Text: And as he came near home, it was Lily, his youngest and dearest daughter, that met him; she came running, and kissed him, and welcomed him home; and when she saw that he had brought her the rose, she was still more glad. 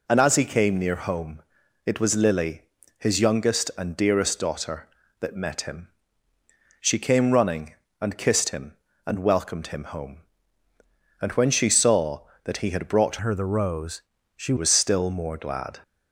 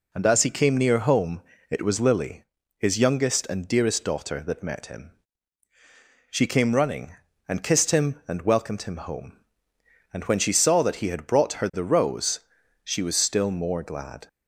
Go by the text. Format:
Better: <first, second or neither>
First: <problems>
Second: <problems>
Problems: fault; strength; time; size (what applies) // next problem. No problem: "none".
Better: second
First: changes voice from "her" to "she"; from 13.2 to 14.5 s; 1.3 s long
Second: none